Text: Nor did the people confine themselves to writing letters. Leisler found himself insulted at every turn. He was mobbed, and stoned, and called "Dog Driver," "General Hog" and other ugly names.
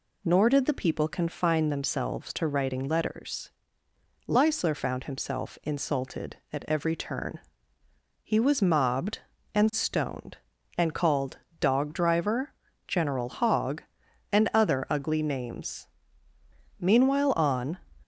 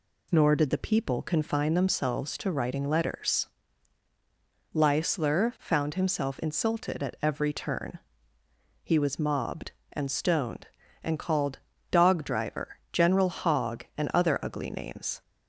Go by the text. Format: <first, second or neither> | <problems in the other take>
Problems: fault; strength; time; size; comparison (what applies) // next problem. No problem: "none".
second | pauses between "called" and "Dog"; slight; at 11.3 s; 0.24 s long; slight in the second // goes on to say "Meanwhile on"; noticeable; from 16.7 s on; 0.98 s long